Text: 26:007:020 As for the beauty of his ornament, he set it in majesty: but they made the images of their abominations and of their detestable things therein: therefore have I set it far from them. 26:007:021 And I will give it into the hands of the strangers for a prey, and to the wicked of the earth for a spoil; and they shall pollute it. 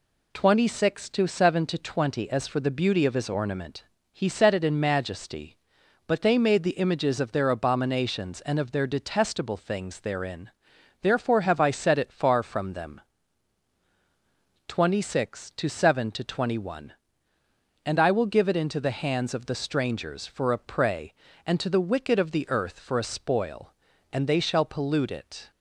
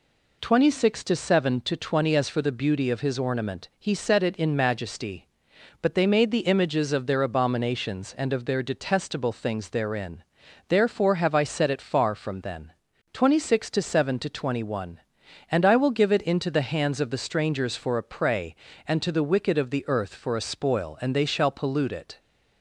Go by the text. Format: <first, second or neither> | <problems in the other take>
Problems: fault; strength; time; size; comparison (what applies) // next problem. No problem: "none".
first | says "then" for "them"; at 12.4 s